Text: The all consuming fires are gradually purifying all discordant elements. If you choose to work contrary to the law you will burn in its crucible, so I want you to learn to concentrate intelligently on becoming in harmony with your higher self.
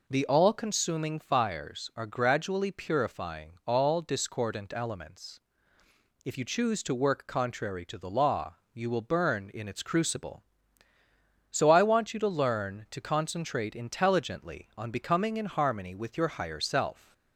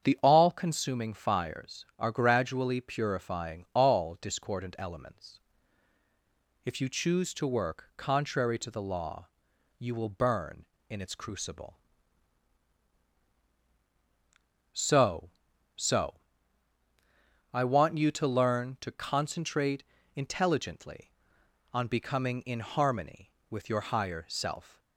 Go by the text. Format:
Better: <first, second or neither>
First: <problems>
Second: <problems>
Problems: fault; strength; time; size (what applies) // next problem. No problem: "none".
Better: first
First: pauses between "law" and "you"; slight; at 8.5 s; 0.18 s long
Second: starts louder than the rest; strong; until 1.0 s; 8 dB // pauses between "law" and "you"; noticeable; at 9.2 s; 0.52 s long // says "so" twice; at 15.7 s // pauses between "concentrate" and "intelligently"; slight; at 19.8 s; 0.30 s long